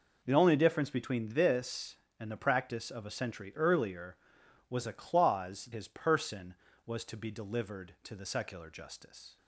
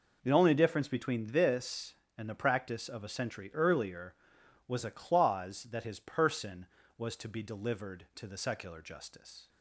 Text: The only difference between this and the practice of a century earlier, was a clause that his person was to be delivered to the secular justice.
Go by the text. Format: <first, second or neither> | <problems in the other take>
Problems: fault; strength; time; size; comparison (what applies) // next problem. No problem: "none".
second | skips "that"; at 5.7 s